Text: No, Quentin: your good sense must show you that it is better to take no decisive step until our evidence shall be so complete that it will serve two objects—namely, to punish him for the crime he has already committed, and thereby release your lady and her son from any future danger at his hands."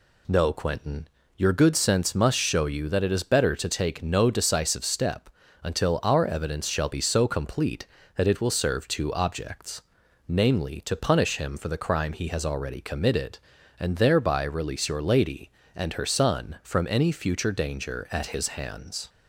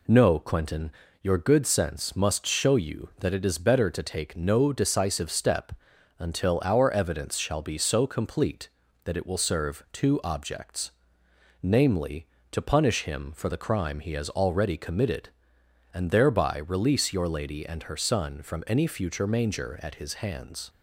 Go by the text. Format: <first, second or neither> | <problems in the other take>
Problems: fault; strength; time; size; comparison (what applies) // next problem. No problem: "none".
first | pauses between "step" and "until"; noticeable; at 5.7 s; 0.48 s long; slight in the first // says "manger" for "danger"; at 19.2 s